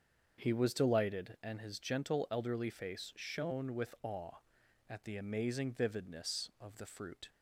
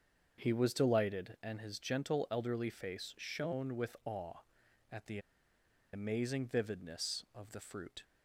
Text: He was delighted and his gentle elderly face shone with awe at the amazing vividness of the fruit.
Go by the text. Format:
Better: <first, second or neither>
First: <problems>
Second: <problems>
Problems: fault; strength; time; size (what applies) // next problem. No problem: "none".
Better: first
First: starts louder than the rest; until 1.4 s; 7 dB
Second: starts louder than the rest; until 1.4 s; 7 dB // pauses between "the" and "amazing"; noticeable; at 5.1 s; 0.74 s long